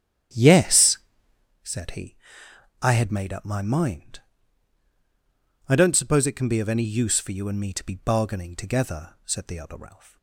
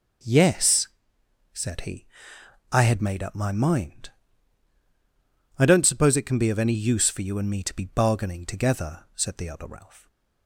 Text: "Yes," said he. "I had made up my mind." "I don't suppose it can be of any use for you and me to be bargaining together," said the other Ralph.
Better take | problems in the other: second | starts louder than the rest; strong; until 1.6 s; 10 dB

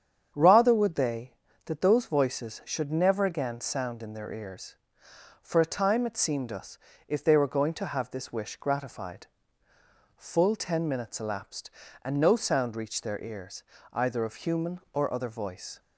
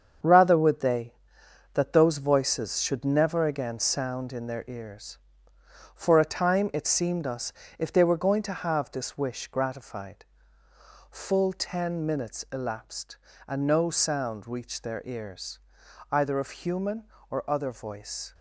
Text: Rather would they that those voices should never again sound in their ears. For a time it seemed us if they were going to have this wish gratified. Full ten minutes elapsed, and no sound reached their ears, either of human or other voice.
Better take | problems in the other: first | gets quieter; strong; throughout; 7.5 dB // starts louder than the rest; strong; until 1.8 s; 7 dB; strong in the first // pauses between "us" and "if"; slight; at 7.5 s; 0.26 s long; slight in the first

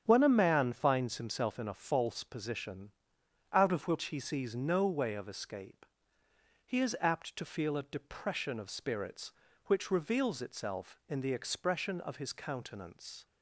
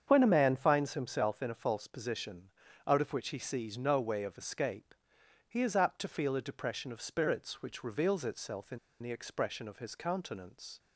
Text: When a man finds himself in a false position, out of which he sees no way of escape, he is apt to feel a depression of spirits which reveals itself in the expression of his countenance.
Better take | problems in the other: first | starts louder than the rest; strong; until 1.0 s; 8 dB; strong in the first // pauses between "in" and "the"; slight; at 8.7 s; 0.23 s long

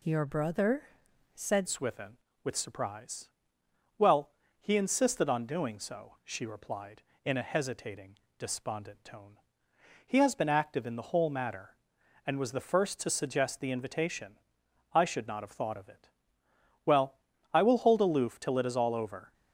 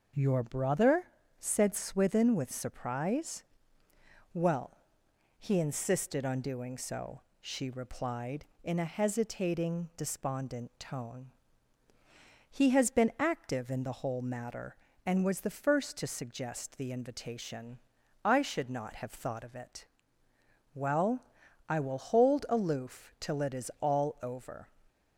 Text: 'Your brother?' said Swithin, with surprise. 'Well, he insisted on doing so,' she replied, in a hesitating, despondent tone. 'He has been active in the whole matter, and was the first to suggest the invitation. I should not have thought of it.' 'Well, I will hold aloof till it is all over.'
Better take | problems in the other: second | changes voice at "Swithin"; from 1.6 s on; 17.7 s long

